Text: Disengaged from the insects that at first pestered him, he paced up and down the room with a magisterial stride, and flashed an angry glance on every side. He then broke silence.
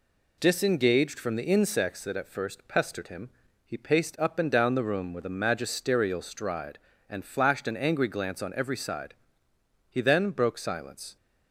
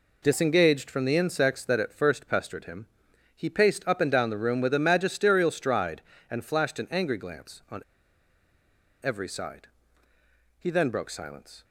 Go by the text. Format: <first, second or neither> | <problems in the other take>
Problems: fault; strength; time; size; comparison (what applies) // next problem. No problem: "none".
first | pauses between "on" and "every"; at 7.8 s; 1.2 s long